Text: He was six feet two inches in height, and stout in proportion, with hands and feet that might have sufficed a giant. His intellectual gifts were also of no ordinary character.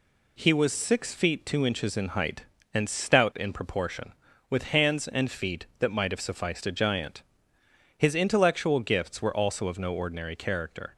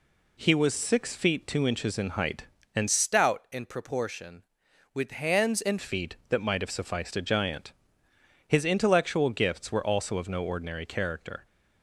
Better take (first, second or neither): first